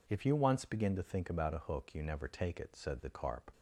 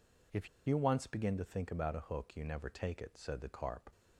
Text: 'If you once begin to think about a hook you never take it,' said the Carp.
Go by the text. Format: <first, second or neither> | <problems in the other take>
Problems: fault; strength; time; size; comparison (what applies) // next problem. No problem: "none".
first | pauses between "If" and "you"; slight; at 0.4 s; 0.18 s long